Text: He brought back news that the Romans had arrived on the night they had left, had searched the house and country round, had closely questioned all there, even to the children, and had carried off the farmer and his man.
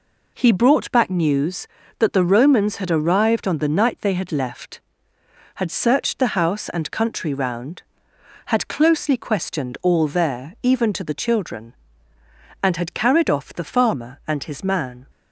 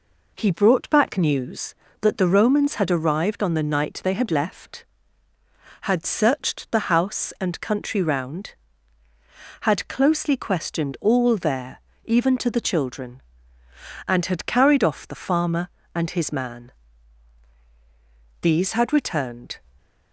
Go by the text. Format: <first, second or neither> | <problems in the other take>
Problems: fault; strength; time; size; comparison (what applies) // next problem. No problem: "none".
first | goes on to say "These had returned"; noticeable; from 18.4 s on; 1.1 s long